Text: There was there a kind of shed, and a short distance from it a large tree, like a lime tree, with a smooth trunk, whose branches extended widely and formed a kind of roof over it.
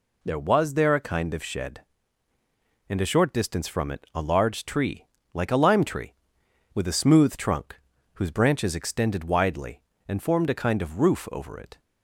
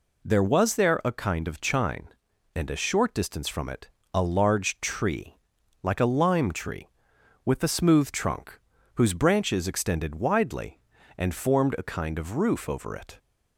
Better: first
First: none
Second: says "chine" for "shed"; at 1.6 s // pauses between "it" and "a"; slight; at 3.8 s; 0.26 s long

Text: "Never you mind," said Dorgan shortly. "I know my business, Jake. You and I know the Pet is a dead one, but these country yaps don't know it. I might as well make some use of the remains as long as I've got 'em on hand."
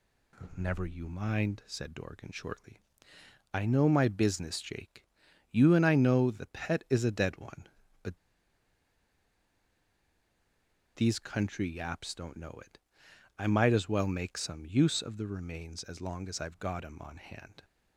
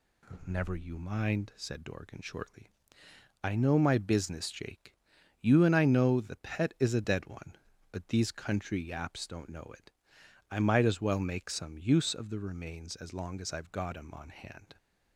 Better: second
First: pauses between "but" and "these"; strong; at 8.1 s; 2.7 s long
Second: none

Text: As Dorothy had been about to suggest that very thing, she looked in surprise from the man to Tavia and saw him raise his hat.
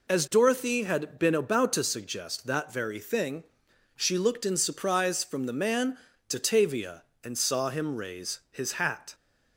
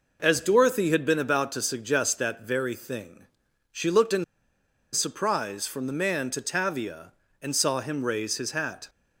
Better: first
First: none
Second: pauses between "in" and "surprise"; noticeable; at 4.2 s; 0.70 s long

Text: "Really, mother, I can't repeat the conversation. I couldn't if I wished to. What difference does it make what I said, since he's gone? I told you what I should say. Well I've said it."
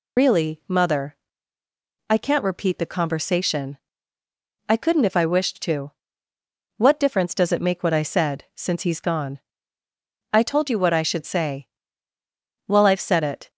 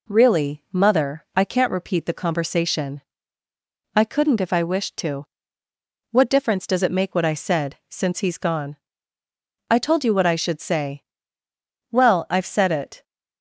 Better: second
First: loses the start of "Really"; at 0.1 s; 90 ms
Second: none

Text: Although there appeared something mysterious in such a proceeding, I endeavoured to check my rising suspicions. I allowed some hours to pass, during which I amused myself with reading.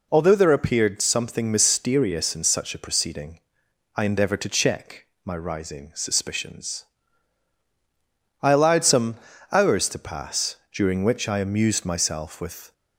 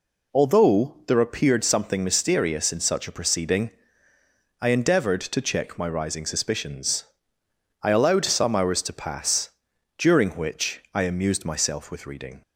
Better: second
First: pauses between "check" and "my"; slight; at 5.0 s; 0.18 s long // pauses between "some" and "hours"; slight; at 9.1 s; 0.36 s long // stops before "reading"; at 12.7 s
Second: none

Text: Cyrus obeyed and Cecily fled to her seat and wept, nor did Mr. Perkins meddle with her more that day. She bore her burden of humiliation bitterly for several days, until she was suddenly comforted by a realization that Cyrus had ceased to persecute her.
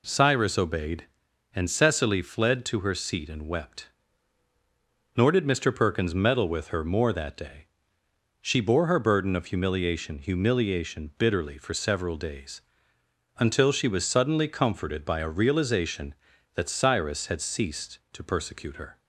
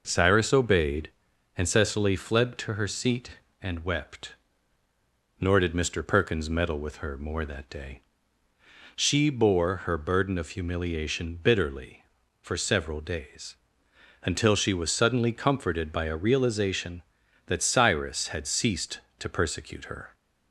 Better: second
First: says "humiliation" twice; at 10.1 s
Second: none

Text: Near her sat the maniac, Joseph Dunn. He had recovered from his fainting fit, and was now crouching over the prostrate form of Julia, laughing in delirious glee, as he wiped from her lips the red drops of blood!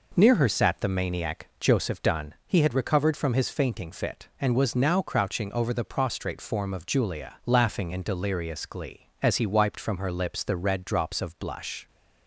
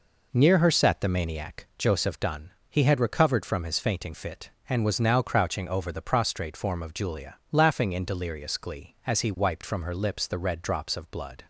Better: second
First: says "blush" for "blood"; at 11.3 s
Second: none

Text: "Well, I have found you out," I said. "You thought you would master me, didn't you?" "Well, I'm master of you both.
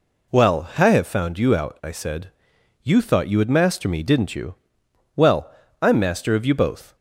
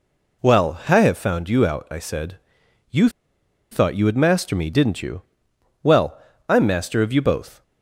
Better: first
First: none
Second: pauses between "You" and "thought"; noticeable; at 3.0 s; 0.62 s long

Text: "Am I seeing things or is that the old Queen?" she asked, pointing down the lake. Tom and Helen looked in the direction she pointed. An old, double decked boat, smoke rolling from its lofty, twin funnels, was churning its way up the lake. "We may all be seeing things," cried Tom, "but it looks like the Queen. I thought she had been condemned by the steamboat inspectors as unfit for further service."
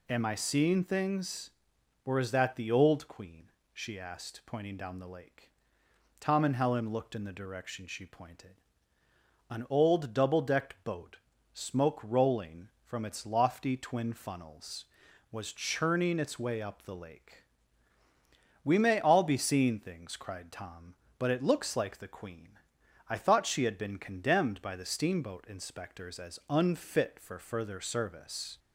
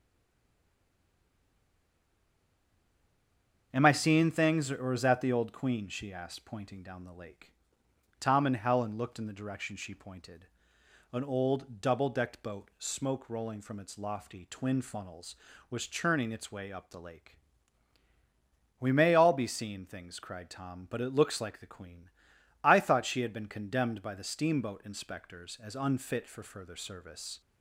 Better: first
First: none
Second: stays silent before the first word; strong; until 3.7 s; 3.7 s long // starts louder than the rest; until 4.7 s; 7 dB

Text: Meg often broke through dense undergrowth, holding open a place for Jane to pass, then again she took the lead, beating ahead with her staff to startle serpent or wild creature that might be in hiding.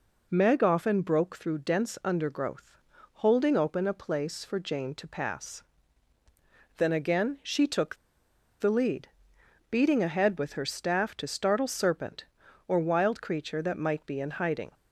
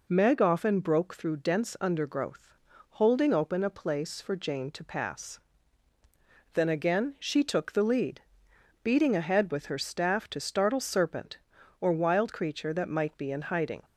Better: second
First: pauses between "took" and "the"; noticeable; at 7.9 s; 0.64 s long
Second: none

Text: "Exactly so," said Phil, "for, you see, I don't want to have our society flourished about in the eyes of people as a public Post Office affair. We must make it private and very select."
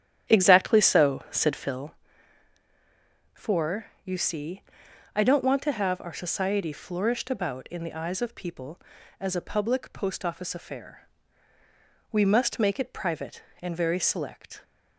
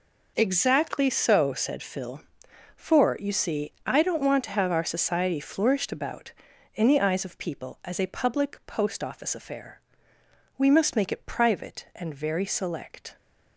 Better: second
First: starts louder than the rest; strong; until 2.0 s; 10 dB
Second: none

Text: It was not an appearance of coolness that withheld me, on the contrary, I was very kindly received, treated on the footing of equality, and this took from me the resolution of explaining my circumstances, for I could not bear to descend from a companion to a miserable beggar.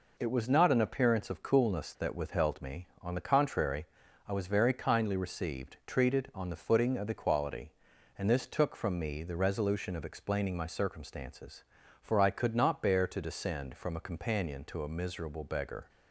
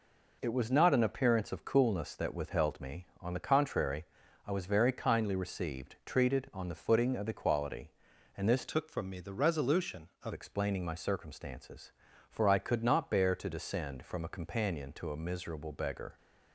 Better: first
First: none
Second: changes voice from "took" to "of"; from 8.6 to 10.3 s; 1.7 s long

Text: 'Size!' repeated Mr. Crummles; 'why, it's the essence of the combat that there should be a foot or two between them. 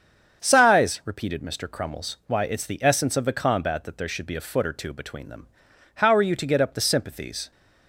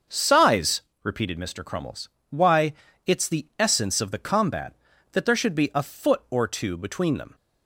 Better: second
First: starts louder than the rest; strong; until 1.4 s; 7 dB // goes on to say "How are you to get up the sympathies"; from 5.9 s on; 1.5 s long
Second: starts louder than the rest; until 1.3 s; 6.5 dB

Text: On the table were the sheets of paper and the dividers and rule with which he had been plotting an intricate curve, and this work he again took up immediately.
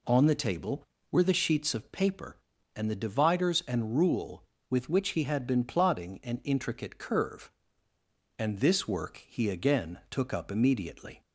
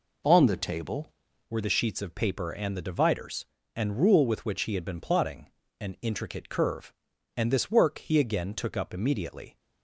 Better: first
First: none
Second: changes voice at "were"; from 1.4 s on; 8.1 s long // pauses between "plotting" and "an"; slight; at 5.4 s; 0.30 s long

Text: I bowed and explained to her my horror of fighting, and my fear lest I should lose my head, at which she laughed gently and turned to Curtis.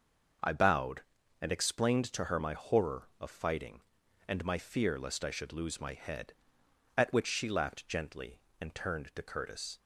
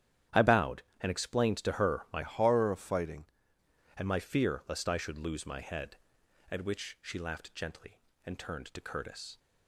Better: first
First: starts louder than the rest; until 1.8 s; 6 dB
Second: starts louder than the rest; strong; until 1.5 s; 10.5 dB // changes voice from "horror" to "fighting"; from 2.2 to 3.2 s; 1.0 s long

